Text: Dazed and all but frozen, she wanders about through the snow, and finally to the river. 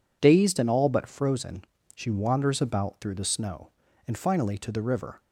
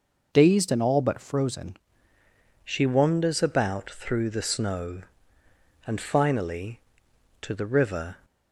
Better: first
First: none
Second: changes voice at "she"; from 2.6 s on; 5.5 s long

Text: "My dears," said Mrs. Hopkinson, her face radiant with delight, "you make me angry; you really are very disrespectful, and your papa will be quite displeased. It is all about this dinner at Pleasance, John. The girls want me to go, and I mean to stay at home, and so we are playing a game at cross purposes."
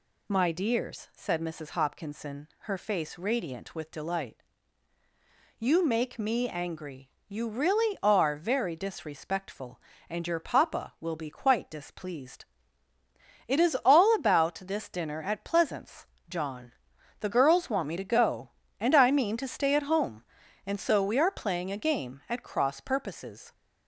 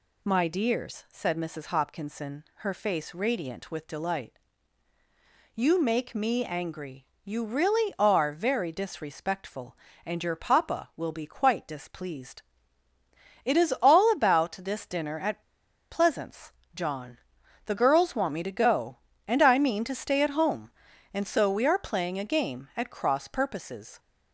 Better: first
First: none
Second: pauses between "at" and "Pleasance"; noticeable; at 15.4 s; 0.50 s long

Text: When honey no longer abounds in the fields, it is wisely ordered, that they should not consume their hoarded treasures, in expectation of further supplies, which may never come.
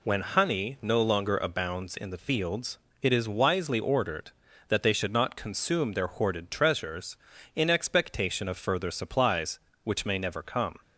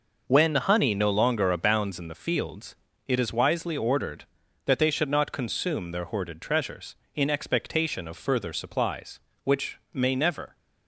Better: first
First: none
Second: stops before "come"; at 10.5 s

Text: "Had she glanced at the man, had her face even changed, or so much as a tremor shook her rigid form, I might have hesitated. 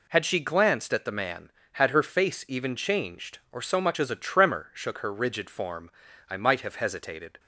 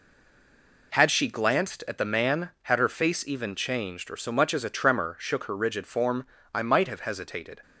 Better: first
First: none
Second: stays silent before the first word; slight; until 0.9 s; 0.9 s long

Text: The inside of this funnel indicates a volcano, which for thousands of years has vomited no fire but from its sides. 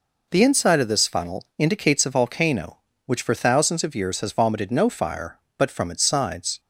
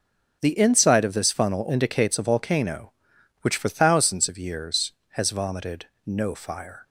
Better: first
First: none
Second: starts louder than the rest; strong; until 1.4 s; 7.5 dB // pauses between "vomited" and "no"; slight; at 5.8 s; 0.20 s long // stops before "but from its sides"; at 6.8 s

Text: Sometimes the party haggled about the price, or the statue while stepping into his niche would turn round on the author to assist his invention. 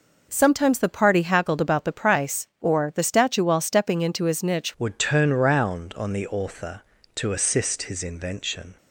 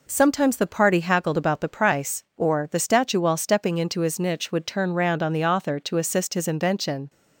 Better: second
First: changes voice at "would"; from 4.7 s on; 4.0 s long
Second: none

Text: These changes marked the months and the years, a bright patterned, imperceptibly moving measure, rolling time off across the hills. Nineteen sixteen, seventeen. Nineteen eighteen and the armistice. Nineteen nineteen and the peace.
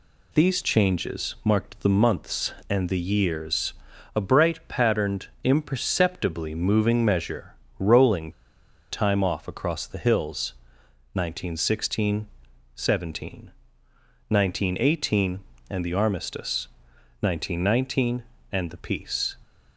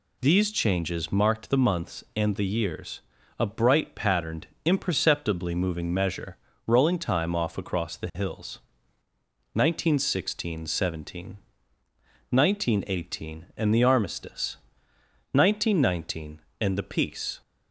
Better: second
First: pauses between "rolling" and "time"; noticeable; at 8.3 s; 0.58 s long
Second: none

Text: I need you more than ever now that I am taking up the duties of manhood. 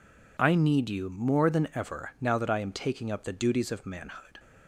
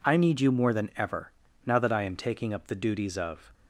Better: first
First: none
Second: pauses between "ever" and "now"; slight; at 1.3 s; 0.36 s long // stops before "manhood"; at 3.5 s

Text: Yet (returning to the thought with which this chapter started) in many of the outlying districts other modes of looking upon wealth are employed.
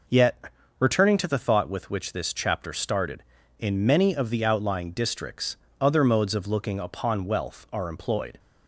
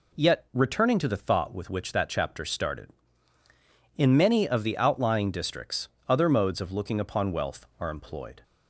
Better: first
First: pauses between "districts" and "other"; slight; at 5.5 s; 0.24 s long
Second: says "that" for "this"; at 1.9 s // pauses between "districts" and "other"; slight; at 5.8 s; 0.20 s long

